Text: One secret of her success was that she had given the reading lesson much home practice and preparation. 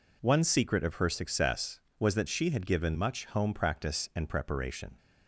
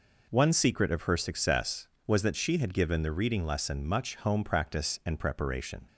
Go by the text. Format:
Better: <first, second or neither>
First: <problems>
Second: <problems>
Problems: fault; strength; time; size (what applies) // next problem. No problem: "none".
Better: second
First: skips "the reading lesson"; at 2.9 s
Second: none